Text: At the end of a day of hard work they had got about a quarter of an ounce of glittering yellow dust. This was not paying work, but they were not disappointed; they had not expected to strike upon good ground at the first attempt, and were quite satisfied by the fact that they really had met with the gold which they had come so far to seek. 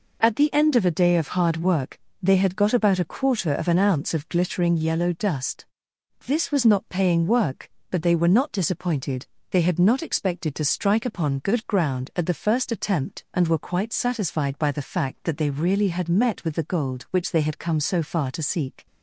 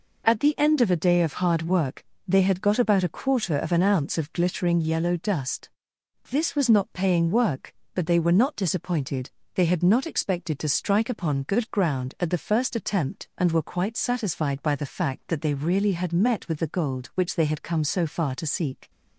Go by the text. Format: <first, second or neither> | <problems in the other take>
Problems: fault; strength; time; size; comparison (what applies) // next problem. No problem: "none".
neither | pauses between "work" and "they"; slight; the same in both